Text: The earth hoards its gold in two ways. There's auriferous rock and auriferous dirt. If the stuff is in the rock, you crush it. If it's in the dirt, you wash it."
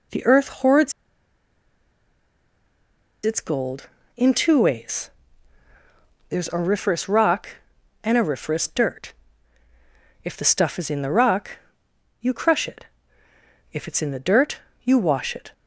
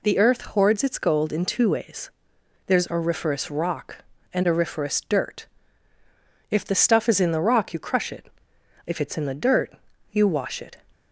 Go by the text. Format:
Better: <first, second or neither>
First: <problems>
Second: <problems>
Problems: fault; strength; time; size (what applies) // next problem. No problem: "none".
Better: second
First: pauses between "hoards" and "its"; strong; at 0.9 s; 2.3 s long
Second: none